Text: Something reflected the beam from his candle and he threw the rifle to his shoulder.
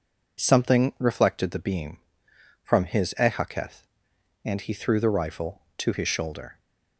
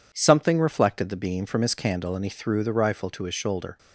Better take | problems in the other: second | says "ehaketh" for "candle"; at 3.1 s

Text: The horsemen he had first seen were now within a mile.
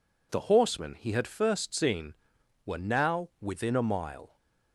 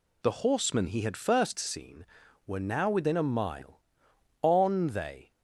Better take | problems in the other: first | goes on to say "On they"; noticeable; from 4.4 s on; 0.90 s long

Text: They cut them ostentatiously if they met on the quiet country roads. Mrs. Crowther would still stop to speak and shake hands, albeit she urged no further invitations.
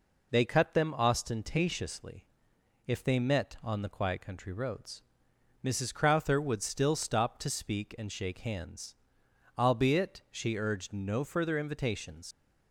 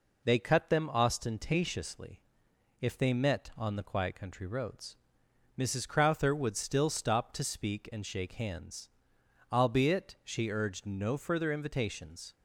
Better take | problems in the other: second | pauses between "ostentatiously" and "if"; noticeable; at 2.2 s; 0.62 s long; noticeable in the second // leaves "invitations" unfinished; at 12.3 s; 100 ms

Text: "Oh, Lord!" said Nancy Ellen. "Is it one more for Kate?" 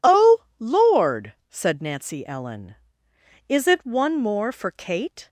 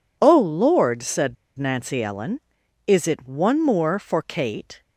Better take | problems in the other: first | pauses between "said" and "Nancy"; slight; at 1.3 s; 0.23 s long

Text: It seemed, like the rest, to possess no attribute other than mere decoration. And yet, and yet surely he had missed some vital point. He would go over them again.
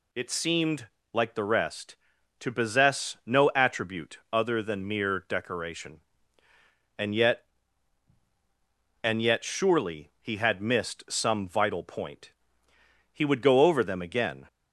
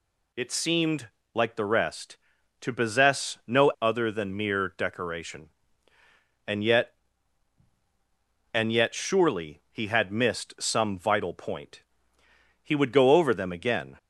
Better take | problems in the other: first | skips "attribute"; at 3.7 s

